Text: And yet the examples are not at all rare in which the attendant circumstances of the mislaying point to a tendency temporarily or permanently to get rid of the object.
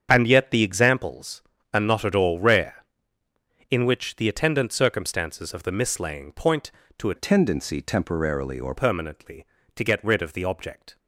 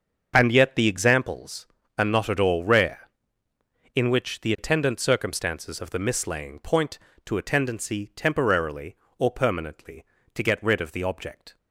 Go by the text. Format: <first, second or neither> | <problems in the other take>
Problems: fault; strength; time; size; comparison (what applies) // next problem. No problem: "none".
second | starts louder than the rest; strong; until 1.1 s; 7.5 dB; also in the second // changes voice from "tendency" to "or"; from 7.1 to 8.7 s; 1.6 s long